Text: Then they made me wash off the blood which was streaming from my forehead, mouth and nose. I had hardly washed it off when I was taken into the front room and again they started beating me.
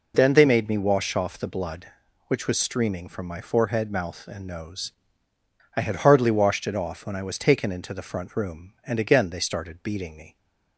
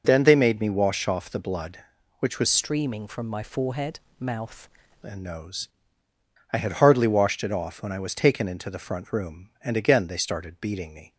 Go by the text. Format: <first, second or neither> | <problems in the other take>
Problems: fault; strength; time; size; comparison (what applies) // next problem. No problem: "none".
first | changes voice from "streaming" to "mouth"; from 2.4 to 4.6 s; 2.2 s long